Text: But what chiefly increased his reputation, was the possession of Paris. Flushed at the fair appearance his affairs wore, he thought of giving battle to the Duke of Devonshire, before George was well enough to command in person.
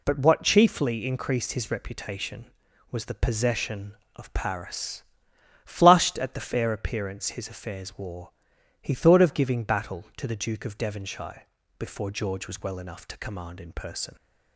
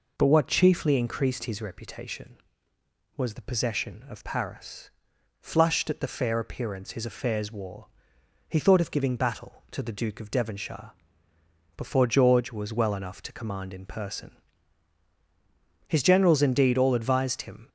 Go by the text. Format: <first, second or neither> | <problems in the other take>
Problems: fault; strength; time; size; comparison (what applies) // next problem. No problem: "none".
first | goes on to say "His generals indeed all advised him"; strong; from 15.8 s on; 1.8 s long